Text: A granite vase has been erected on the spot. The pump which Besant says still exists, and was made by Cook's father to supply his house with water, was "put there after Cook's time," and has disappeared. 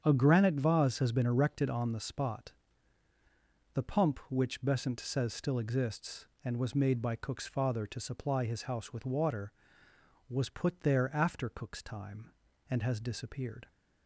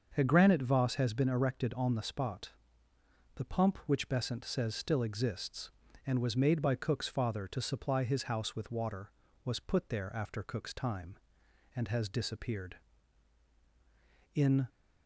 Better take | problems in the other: first | starts louder than the rest; until 1.1 s; 6.5 dB; strong in the first // goes on to say "In"; slight; from 14.3 s on; 0.34 s long

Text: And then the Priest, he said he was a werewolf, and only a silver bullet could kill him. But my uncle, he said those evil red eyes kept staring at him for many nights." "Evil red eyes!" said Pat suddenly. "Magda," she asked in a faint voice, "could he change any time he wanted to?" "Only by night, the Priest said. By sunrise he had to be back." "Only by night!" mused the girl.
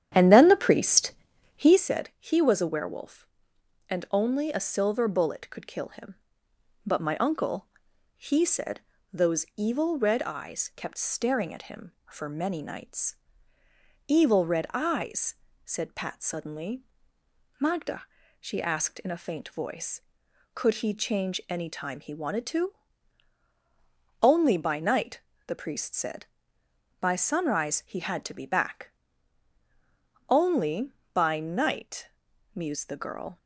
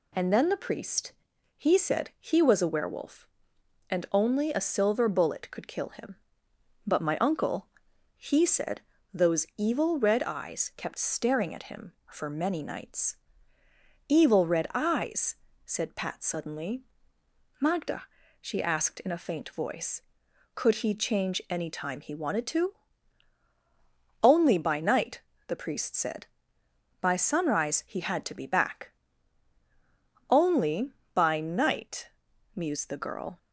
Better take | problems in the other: second | starts louder than the rest; strong; until 1.8 s; 10 dB // pauses between "said" and "those"; slight; at 8.8 s; 0.30 s long; slight in the second

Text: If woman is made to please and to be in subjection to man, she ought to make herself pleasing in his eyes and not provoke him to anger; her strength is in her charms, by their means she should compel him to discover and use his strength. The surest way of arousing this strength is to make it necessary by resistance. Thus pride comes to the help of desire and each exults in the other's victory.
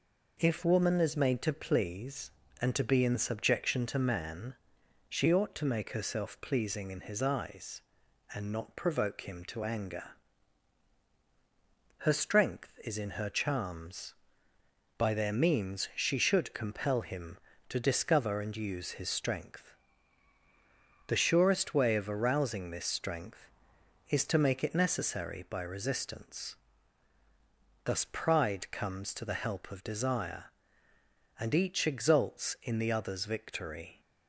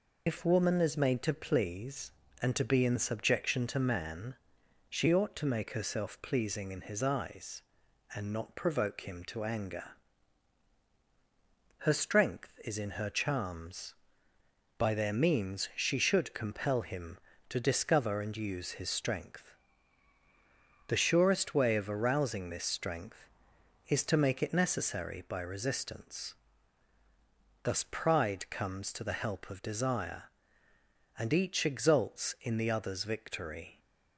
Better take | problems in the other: first | loses the start of "If"; at 0.2 s; 80 ms

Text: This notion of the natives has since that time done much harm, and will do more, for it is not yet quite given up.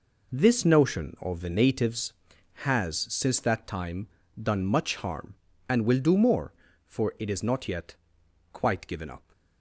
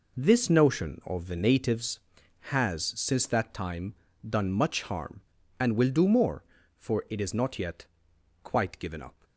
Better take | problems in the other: neither | pauses between "time" and "done"; slight; the same in both // pauses between "yet" and "quite"; noticeable; the same in both

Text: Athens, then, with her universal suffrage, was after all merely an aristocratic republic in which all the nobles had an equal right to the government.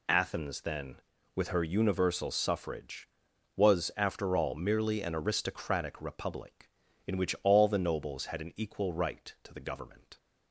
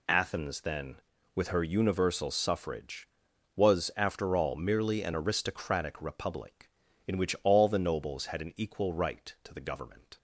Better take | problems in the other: neither | none

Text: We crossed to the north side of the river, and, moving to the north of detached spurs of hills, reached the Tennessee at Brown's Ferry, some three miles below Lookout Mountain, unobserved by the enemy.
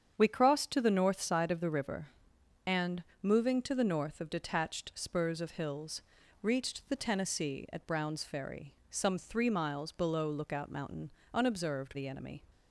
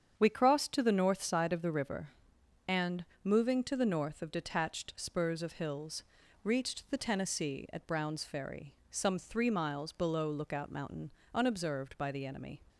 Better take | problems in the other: second | starts louder than the rest; strong; until 1.1 s; 8 dB; strong in the second // skips "by"; at 11.9 s

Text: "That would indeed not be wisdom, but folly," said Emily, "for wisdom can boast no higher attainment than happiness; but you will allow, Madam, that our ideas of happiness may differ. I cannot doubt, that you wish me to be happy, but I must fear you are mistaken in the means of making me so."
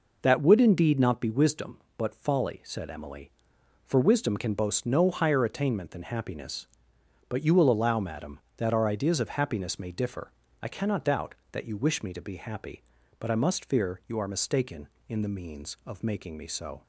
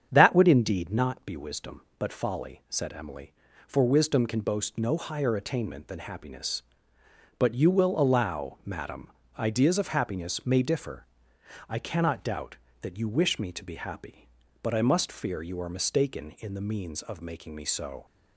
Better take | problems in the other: first | starts louder than the rest; strong; until 1.1 s; 8 dB // skips "that our"; at 9.2 s

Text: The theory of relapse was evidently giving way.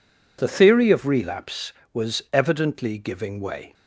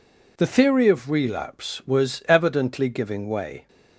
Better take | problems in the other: neither | none

